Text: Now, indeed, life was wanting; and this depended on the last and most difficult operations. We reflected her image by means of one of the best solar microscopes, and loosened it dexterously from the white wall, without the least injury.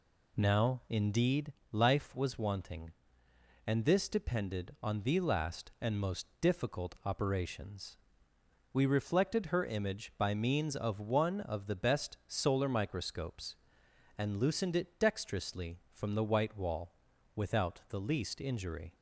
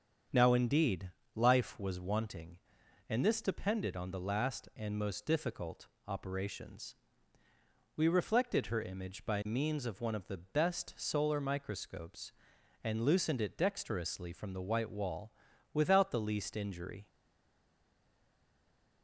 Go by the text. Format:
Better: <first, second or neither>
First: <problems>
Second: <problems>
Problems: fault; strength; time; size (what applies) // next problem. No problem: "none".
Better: first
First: none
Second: starts louder than the rest; strong; until 1.5 s; 7.5 dB // pauses between "difficult" and "operations"; slight; at 5.8 s; 0.18 s long // stays silent after the last word; noticeable; from 17.0 s on; 2.0 s long